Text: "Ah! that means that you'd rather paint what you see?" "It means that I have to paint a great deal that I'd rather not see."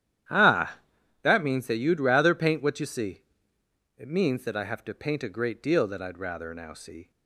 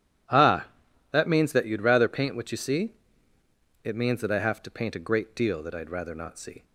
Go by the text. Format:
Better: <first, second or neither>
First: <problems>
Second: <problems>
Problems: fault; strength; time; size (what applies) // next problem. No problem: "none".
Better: second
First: starts louder than the rest; strong; until 1.7 s; 11 dB // says "now" for "not"; at 6.5 s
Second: none